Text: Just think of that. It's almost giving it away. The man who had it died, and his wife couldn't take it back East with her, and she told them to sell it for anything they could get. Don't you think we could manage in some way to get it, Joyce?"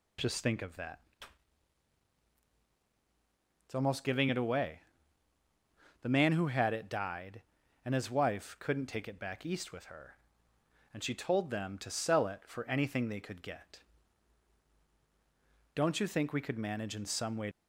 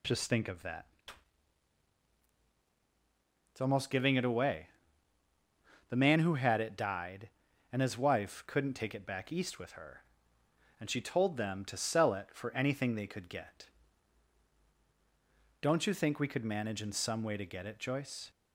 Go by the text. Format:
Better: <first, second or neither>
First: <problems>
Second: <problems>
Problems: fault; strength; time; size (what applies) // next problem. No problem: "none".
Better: second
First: stops before "to get it Joyce"; at 17.5 s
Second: none